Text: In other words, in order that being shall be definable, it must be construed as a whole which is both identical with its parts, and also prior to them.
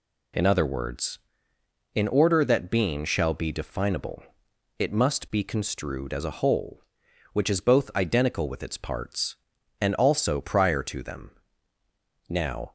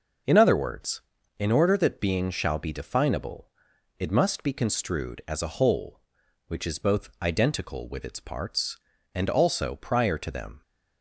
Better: second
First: goes on to say "Now"; slight; from 12.2 s on; 0.42 s long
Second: none

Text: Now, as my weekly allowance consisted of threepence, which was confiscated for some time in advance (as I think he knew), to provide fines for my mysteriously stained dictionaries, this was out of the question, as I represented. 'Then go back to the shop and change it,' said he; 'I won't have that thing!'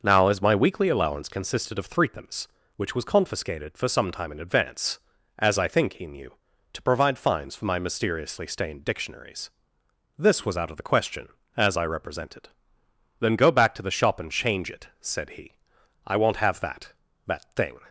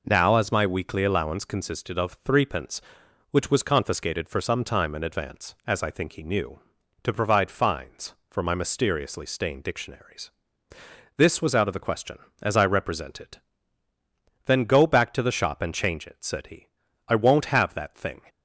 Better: second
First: starts louder than the rest; noticeable; until 1.0 s; 6 dB // says "that" twice; at 17.2 s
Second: none

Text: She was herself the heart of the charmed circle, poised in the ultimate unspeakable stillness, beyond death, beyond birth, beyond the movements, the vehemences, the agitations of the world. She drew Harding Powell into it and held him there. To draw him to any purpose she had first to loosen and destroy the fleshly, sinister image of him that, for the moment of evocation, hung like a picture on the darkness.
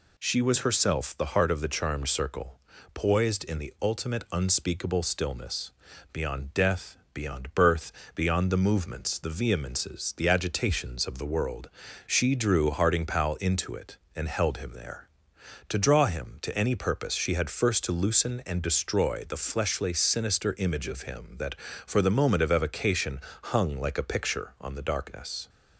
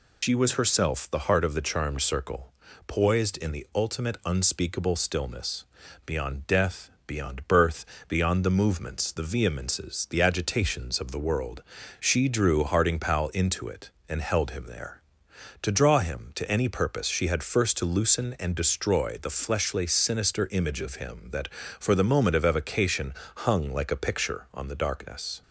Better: first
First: none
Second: loses the start of "She"; at 0.2 s; 105 ms

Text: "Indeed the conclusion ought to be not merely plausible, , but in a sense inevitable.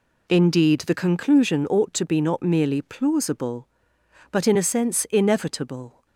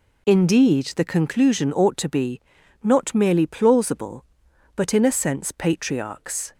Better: first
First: none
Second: pauses between "be" and "not"; at 2.3 s; 0.44 s long // says "patriarchs" for "inevitable"; at 5.5 s

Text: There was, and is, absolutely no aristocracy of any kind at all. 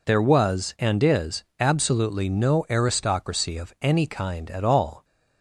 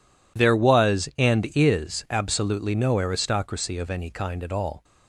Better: neither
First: none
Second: none

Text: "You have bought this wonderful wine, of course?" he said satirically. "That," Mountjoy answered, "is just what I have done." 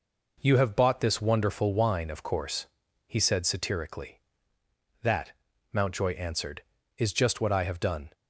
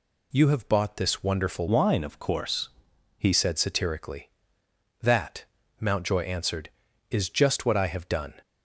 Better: first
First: none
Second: changes voice from "wine" to "he"; from 1.6 to 3.3 s; 1.7 s long

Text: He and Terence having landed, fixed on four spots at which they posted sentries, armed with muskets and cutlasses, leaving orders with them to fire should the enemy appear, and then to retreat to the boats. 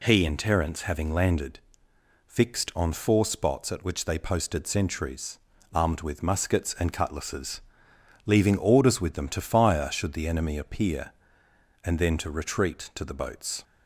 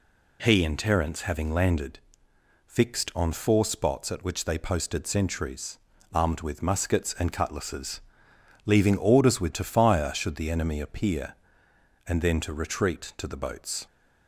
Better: first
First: none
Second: skips "them"; at 9.5 s

